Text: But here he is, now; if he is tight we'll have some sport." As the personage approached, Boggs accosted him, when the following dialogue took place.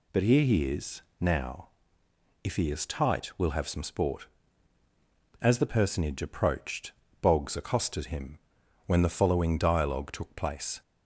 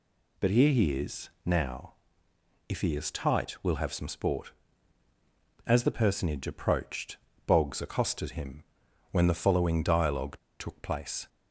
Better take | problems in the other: first | pauses between "dialogue" and "took"; slight; at 10.3 s; 0.23 s long

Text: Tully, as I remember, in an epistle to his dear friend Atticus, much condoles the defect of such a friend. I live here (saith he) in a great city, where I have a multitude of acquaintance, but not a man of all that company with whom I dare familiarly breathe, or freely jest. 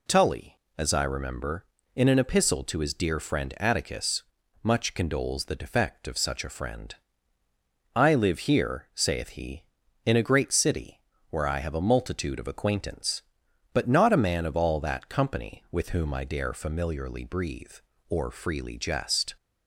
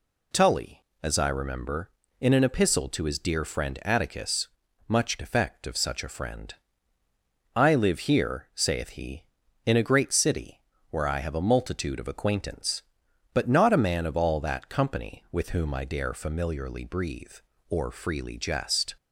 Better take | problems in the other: first | skips "condoles the"; at 5.1 s

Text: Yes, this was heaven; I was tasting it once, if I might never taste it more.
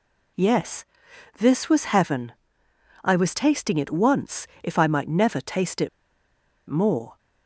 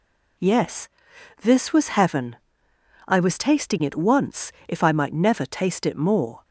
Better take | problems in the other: second | pauses between "it" and "more"; noticeable; at 5.8 s; 0.80 s long

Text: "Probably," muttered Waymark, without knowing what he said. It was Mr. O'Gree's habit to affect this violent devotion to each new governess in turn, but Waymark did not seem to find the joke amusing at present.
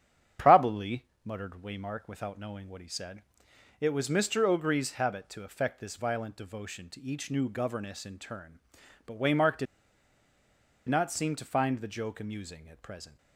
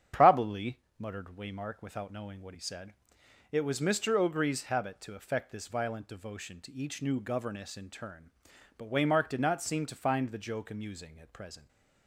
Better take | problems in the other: second | starts louder than the rest; strong; until 1.5 s; 9 dB; strong in the second // pauses between "did" and "not"; at 9.6 s; 1.2 s long

